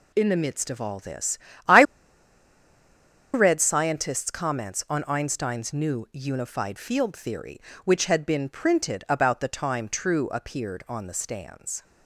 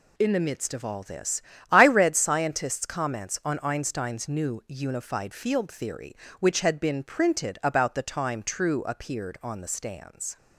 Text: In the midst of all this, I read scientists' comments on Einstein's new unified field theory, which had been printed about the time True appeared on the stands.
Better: second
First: pauses between "I" and "read"; strong; at 1.8 s; 1.5 s long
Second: none

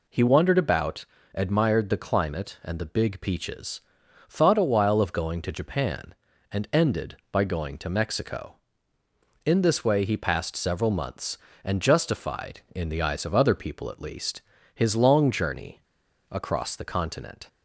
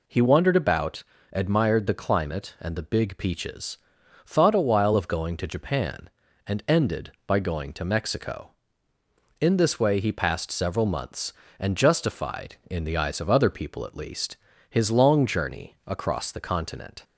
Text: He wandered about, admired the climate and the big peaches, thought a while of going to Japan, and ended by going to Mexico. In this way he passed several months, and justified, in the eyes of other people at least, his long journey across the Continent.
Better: second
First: pauses between "journey" and "across"; noticeable; at 15.8 s; 0.49 s long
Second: none

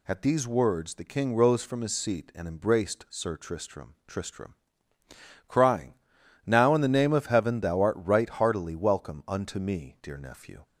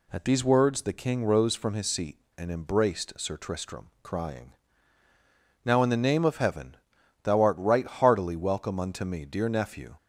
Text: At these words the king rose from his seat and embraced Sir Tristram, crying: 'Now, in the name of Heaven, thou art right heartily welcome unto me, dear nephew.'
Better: second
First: says "Tristram" twice; at 4.0 s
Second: none

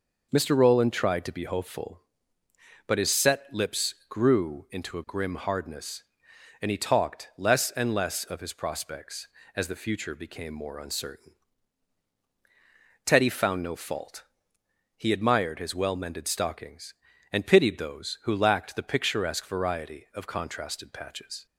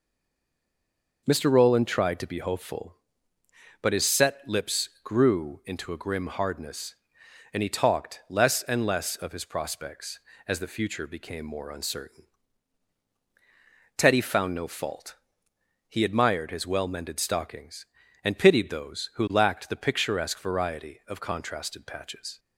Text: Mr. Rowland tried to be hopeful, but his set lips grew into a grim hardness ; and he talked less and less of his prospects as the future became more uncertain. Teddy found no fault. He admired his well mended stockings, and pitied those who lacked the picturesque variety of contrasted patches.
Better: first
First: pauses between "lips" and "grew"; slight; at 3.9 s; 0.16 s long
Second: stays silent before the first word; noticeable; until 1.2 s; 1.2 s long // pauses between "lips" and "grew"; slight; at 4.8 s; 0.16 s long

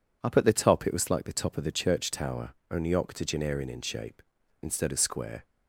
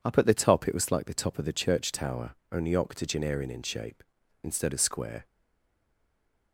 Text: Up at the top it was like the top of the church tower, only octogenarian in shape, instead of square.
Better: first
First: none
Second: stays silent after the last word; noticeable; from 5.2 s on; 1.3 s long

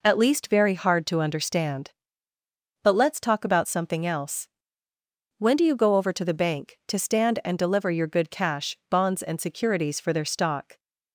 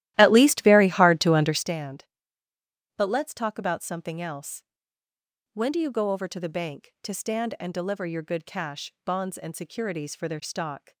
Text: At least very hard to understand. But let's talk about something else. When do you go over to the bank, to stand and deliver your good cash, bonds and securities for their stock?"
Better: first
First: none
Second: starts louder than the rest; strong; until 1.7 s; 14.5 dB

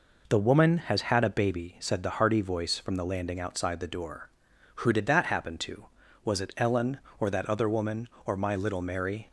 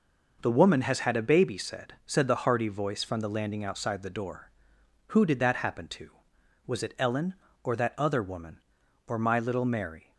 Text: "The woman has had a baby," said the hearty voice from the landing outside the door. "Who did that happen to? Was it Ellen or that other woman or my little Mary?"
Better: first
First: none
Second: says "said" twice; at 2.0 s

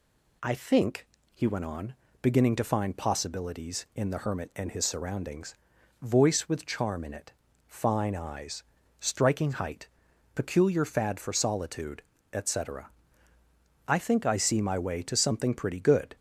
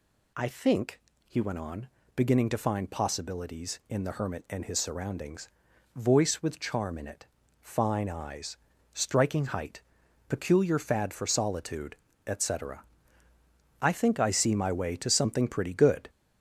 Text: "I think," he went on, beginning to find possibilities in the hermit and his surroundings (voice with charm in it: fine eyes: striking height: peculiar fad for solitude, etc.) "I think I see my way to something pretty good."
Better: first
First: none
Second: gets louder; noticeable; throughout; 5 dB

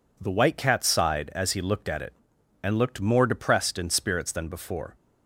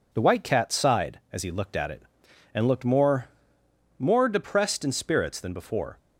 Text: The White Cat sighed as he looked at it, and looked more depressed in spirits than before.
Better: first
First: none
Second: says "more" twice; at 3.9 s

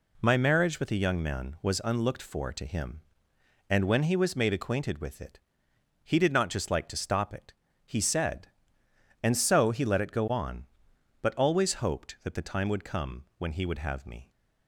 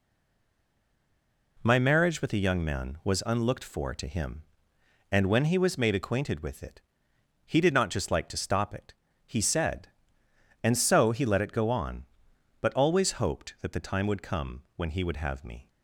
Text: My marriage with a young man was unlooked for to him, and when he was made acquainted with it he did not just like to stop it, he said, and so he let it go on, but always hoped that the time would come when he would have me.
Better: first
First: pauses between "it" and "he"; noticeable; at 5.3 s; 0.64 s long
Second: stays silent before the first word; noticeable; until 1.5 s; 1.5 s long // pauses between "it" and "he"; noticeable; at 6.7 s; 0.64 s long

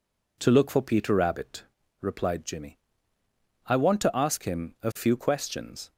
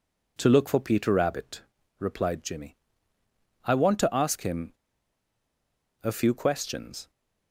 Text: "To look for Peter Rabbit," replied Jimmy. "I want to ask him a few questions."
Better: first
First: none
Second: pauses between "him" and "a"; strong; at 4.7 s; 1.3 s long

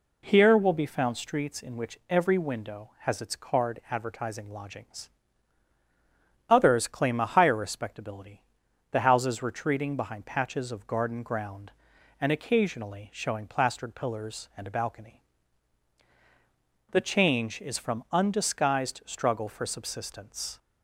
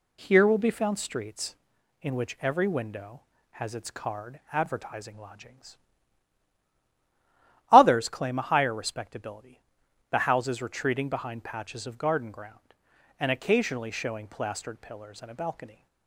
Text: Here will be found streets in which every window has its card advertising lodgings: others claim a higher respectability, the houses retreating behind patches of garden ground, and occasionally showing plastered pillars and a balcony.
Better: second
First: goes on to say "The change is from undisguised struggle for subsistence"; strong; from 16.9 s on; 3.6 s long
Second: none

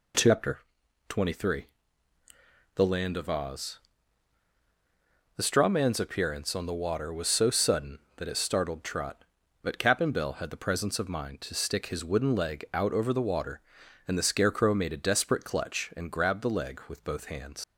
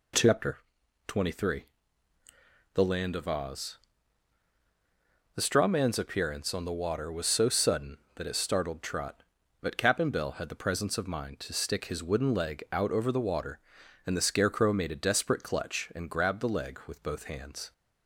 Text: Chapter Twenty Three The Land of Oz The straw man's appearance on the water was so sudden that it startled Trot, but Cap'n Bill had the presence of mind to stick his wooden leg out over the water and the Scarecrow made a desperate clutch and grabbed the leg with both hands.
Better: second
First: pauses between "Chapter" and "Twenty"; noticeable; at 0.5 s; 0.50 s long // pauses between "Three" and "The"; at 1.6 s; 1.1 s long // pauses between "Oz" and "The"; strong; at 3.7 s; 1.5 s long // leaves "hands" unfinished; at 17.6 s; 100 ms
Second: pauses between "Chapter" and "Twenty"; noticeable; at 0.5 s; 0.50 s long // pauses between "Three" and "The"; at 1.6 s; 1.1 s long // pauses between "Oz" and "The"; strong; at 3.7 s; 1.5 s long

